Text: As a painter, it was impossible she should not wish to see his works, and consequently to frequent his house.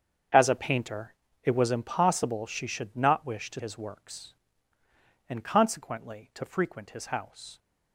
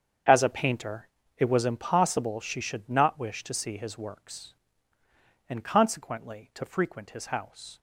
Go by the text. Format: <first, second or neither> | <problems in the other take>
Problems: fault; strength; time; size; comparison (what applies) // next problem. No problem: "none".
second | starts louder than the rest; strong; until 1.6 s; 7.5 dB; strong in the second // skips "see"; at 3.5 s